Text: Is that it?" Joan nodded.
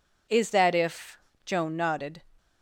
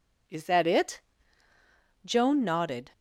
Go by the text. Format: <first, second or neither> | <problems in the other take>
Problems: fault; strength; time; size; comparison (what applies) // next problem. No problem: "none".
second | says "if" for "it"; at 0.7 s